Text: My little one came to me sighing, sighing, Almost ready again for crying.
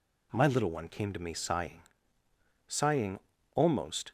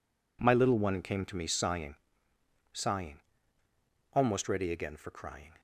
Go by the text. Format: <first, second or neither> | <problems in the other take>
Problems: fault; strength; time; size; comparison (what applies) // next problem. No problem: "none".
second | stops before "ready again for crying"; at 4.0 s